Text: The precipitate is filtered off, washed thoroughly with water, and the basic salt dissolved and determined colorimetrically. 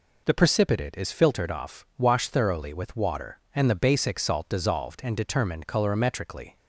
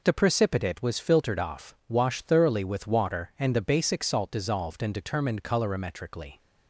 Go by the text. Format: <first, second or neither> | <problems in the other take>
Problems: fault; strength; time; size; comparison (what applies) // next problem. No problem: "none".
first | says "was" for "is"; at 0.8 s